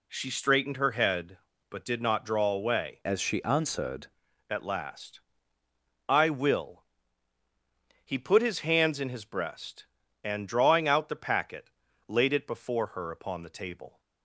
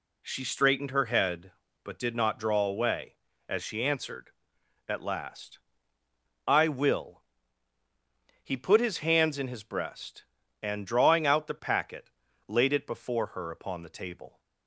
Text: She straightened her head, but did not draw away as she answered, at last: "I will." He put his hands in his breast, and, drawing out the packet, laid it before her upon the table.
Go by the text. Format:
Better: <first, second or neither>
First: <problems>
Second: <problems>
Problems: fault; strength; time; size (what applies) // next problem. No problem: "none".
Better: second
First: changes voice from "as" to "answered"; from 3.0 to 4.0 s; 1.0 s long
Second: none